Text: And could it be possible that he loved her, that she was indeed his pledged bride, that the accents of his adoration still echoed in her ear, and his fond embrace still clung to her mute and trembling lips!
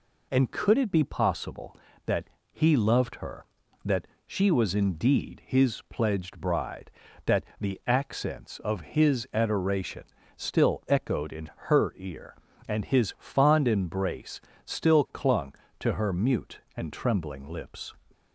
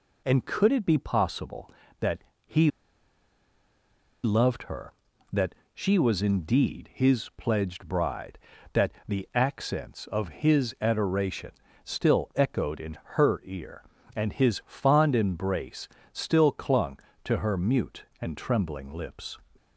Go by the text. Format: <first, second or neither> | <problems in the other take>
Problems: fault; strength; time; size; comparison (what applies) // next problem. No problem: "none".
first | pauses between "that" and "he"; slight; at 2.1 s; 0.26 s long; slight in the first // pauses between "he" and "loved"; strong; at 2.7 s; 1.5 s long // pauses between "that" and "she"; slight; at 5.5 s; 0.20 s long; slight in the first // pauses between "that" and "the"; slight; at 8.9 s; 0.16 s long; slight in the first // pauses between "adoration" and "still"; slight; at 11.5 s; 0.32 s long; slight in the first // pauses between "in" and "her"; slight; at 12.9 s; 0.18 s long; slight in the first // pauses between "embrace" and "still"; slight; at 15.8 s; 0.24 s long; slight in the first